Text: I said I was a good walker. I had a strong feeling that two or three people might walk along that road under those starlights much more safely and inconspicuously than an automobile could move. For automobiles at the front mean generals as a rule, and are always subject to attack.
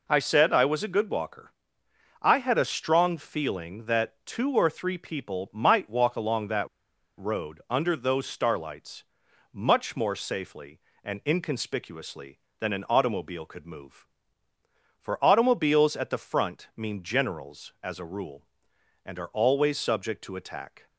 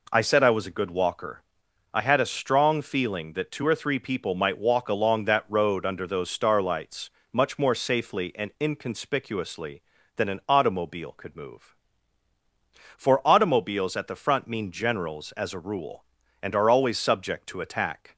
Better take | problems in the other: second | pauses between "that" and "road"; noticeable; at 6.6 s; 0.51 s long // pauses between "starlights" and "much"; noticeable; at 9.0 s; 0.48 s long; slight in the second

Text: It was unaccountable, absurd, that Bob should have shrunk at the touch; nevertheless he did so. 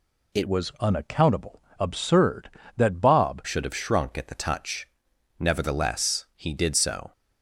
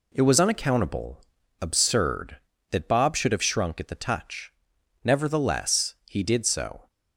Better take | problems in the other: second | changes voice from "was" to "Bob"; from 0.4 to 3.4 s; 3.0 s long

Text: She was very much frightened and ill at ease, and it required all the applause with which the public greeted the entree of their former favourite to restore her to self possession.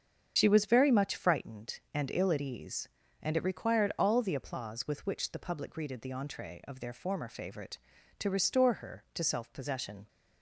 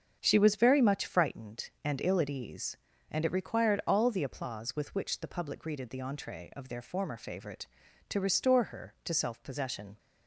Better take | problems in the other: second | loses the start of "She"; at 0.3 s; 55 ms // starts louder than the rest; strong; until 1.3 s; 7.5 dB; strong in the second

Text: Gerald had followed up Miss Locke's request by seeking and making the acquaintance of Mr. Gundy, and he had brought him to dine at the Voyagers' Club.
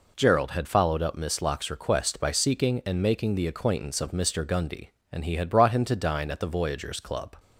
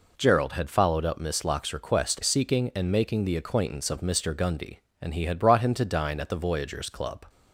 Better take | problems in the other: first | skips "by"; at 2.2 s

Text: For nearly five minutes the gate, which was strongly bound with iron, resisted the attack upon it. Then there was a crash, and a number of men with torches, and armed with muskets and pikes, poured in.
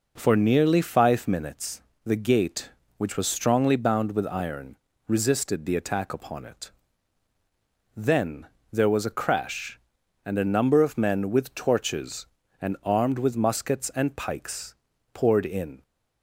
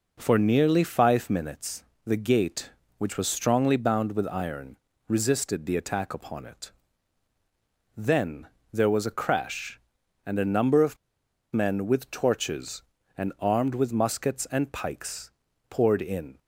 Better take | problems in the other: first | pauses between "minutes" and "the"; slight; at 1.8 s; 0.20 s long; slight in the first // pauses between "Then" and "there"; slight; at 8.4 s; 0.26 s long; slight in the first // pauses between "of" and "men"; noticeable; at 10.9 s; 0.57 s long

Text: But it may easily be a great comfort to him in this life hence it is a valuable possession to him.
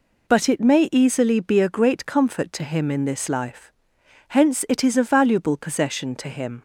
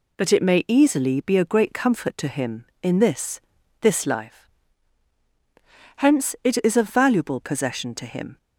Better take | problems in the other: first | says "this" twice; at 3.8 s // pauses between "life" and "hence"; strong; at 4.4 s; 1.4 s long; noticeable in the first

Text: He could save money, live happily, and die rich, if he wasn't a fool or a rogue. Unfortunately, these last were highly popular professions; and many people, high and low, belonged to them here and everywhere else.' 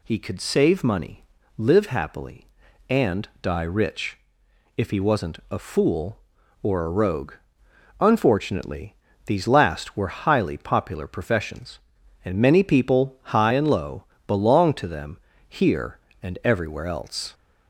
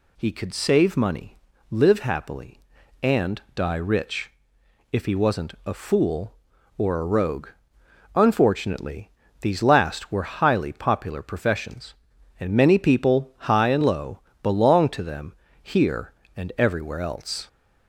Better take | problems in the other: neither | pauses between "them" and "here"; slight; the same in both

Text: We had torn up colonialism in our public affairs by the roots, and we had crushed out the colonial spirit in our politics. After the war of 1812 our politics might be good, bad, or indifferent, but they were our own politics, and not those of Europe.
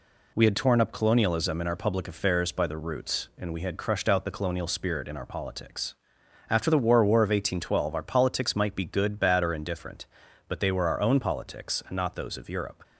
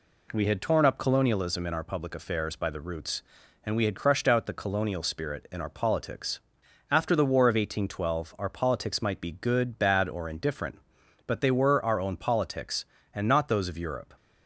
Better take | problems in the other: second | says "war" twice; at 7.0 s

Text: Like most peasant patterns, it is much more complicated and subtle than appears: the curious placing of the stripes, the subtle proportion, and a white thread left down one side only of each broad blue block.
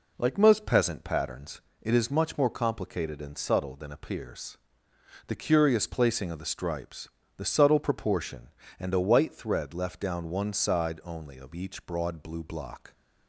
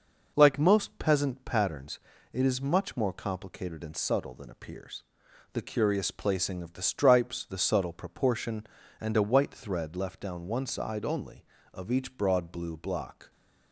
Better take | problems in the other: neither | none

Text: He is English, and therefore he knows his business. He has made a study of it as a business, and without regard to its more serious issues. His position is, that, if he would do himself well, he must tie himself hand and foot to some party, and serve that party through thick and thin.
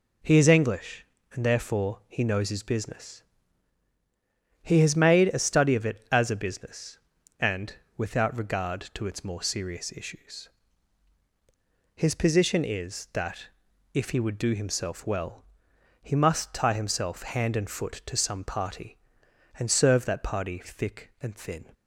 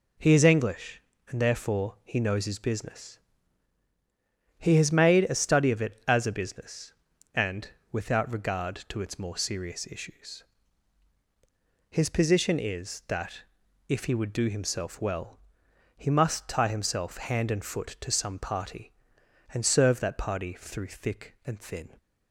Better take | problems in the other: second | pauses between "and" and "without"; slight; at 7.7 s; 0.24 s long; slight in the second // skips "through"; at 20.6 s

